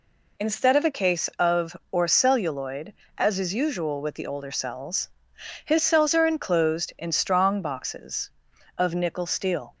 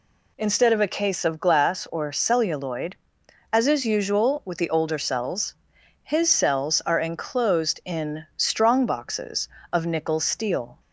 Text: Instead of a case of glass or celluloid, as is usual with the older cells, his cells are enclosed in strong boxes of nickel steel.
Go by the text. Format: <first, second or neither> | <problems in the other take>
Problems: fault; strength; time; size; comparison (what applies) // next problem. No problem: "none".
second | skips "glass"; at 1.8 s